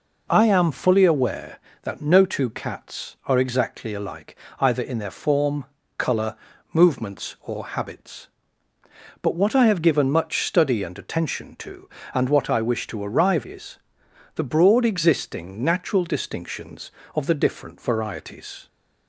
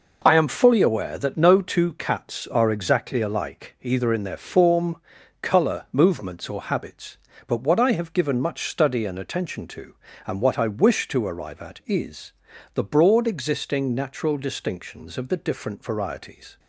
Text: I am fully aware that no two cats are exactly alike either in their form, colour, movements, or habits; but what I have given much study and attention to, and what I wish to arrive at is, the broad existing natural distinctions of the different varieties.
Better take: second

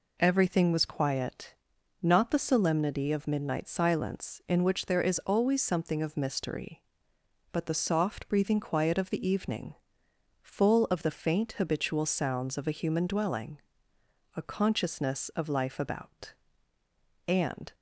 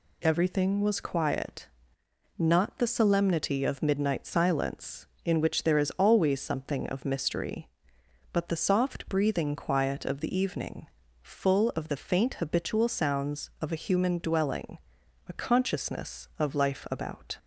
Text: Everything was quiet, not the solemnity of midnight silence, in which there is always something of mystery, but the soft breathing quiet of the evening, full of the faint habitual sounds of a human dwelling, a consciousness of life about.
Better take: second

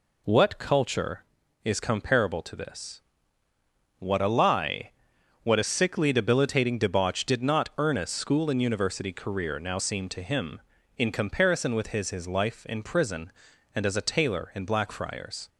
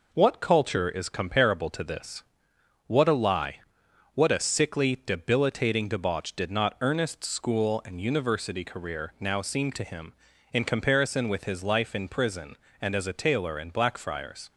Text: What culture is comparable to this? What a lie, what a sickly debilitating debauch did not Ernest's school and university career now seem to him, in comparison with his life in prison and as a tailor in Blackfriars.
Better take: second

